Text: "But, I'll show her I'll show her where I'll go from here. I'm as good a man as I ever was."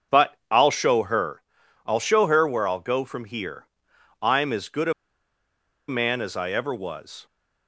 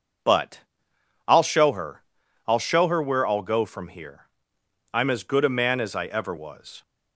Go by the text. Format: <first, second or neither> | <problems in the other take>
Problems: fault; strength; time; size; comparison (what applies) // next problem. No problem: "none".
second | starts louder than the rest; until 1.2 s; 6.5 dB // pauses between "her" and "I'll"; at 1.4 s; 0.42 s long; also in the second // pauses between "a" and "man"; noticeable; at 4.9 s; 0.96 s long